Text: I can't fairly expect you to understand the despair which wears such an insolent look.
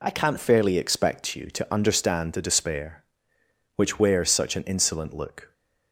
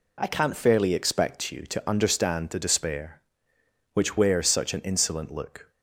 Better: neither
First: none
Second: none

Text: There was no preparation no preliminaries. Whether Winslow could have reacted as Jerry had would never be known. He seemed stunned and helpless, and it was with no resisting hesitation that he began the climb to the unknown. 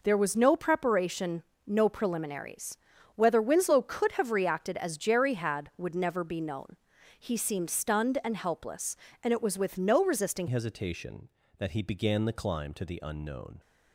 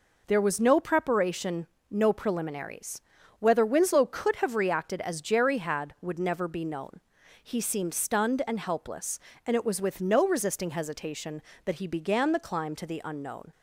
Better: second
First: pauses between "preparation" and "no"; slight; at 1.4 s; 0.24 s long // changes voice at "hesitation"; from 10.4 s on; 3.1 s long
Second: pauses between "preparation" and "no"; slight; at 1.6 s; 0.24 s long

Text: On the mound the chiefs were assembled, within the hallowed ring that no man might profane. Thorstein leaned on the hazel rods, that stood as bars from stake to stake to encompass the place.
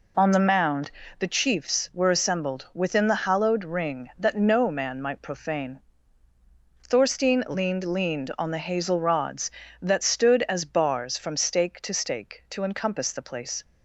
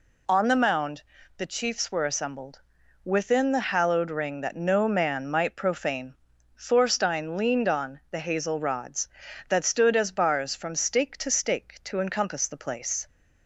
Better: second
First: pauses between "mound" and "the"; slight; at 0.9 s; 0.28 s long // says "leaned" twice; at 7.8 s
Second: pauses between "mound" and "the"; slight; at 1.0 s; 0.34 s long

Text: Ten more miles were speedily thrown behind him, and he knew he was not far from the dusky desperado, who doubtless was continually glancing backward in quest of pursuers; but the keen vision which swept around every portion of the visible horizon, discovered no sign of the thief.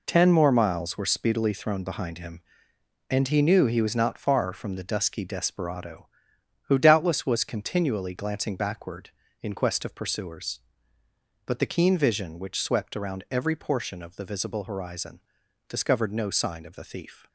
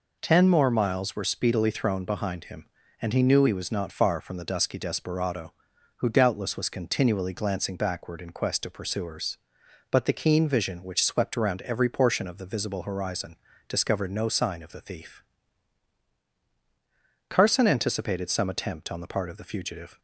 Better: first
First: none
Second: goes on to say "Carson anticipated some attempt on the part of the fugitive"; strong; from 17.2 s on; 2.7 s long

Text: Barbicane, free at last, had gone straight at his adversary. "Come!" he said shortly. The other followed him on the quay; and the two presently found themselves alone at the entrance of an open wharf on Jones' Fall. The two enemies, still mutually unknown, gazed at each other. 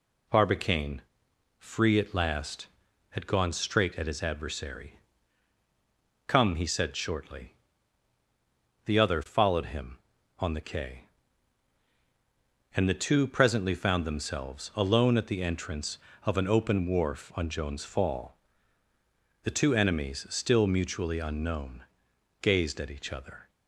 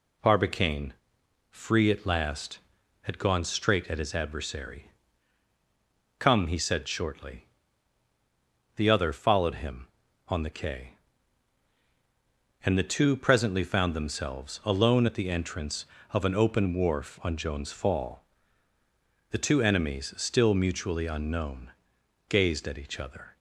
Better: neither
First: none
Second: none

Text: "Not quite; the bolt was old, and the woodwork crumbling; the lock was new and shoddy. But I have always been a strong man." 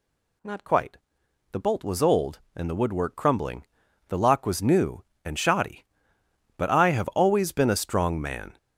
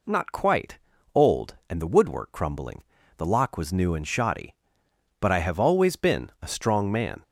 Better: first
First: none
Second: skips "the bolt was"; at 0.9 s

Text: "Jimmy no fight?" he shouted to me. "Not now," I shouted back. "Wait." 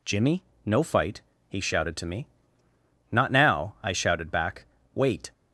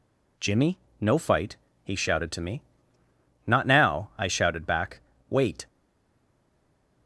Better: first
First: pauses between "Jimmy" and "no"; slight; at 0.4 s; 0.22 s long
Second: pauses between "Jimmy" and "no"; slight; at 0.7 s; 0.22 s long // stays silent after the last word; noticeable; from 5.6 s on; 1.4 s long

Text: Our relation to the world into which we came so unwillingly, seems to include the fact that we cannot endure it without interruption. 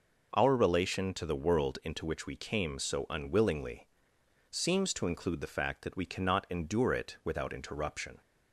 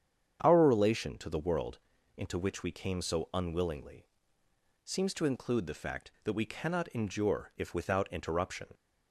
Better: first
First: none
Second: starts louder than the rest; strong; until 1.4 s; 8.5 dB // pauses between "world" and "into"; at 1.7 s; 0.40 s long // says "if" for "it"; at 7.5 s

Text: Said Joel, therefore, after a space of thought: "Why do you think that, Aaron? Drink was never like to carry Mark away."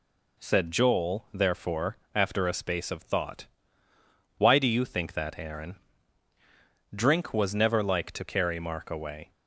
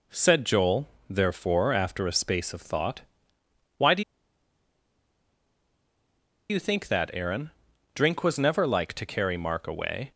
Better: first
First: none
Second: pauses between "do" and "you"; strong; at 4.0 s; 2.4 s long

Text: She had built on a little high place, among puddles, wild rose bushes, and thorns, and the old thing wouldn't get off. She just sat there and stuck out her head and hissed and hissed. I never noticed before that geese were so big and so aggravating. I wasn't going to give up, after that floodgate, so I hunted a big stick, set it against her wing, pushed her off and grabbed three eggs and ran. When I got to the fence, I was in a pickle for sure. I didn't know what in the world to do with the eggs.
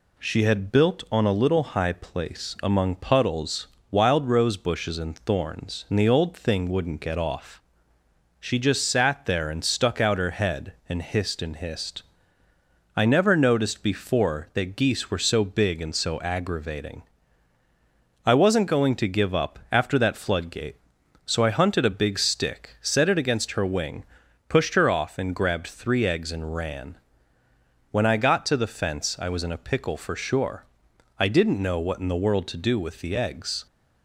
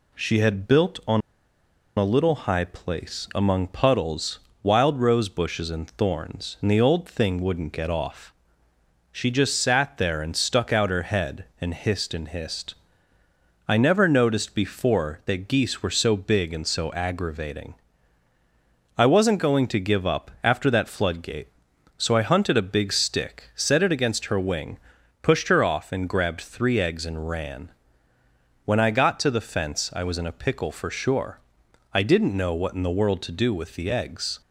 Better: first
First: none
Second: pauses between "on" and "a"; noticeable; at 1.2 s; 0.76 s long

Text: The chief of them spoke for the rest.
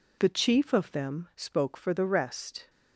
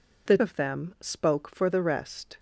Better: first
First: none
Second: skips "chief"; at 0.3 s

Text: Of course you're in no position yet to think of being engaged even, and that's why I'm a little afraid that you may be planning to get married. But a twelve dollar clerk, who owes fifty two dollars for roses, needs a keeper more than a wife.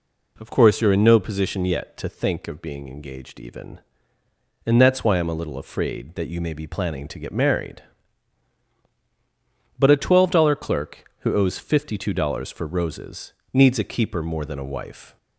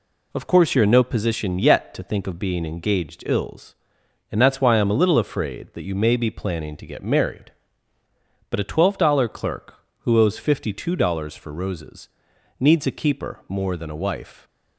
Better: first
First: none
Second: says "ills" for "even"; at 3.2 s

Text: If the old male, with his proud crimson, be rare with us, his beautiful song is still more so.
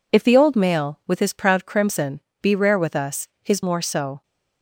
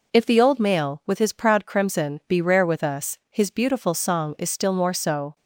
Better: second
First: skips "beautiful song is still"; at 3.6 s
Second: none

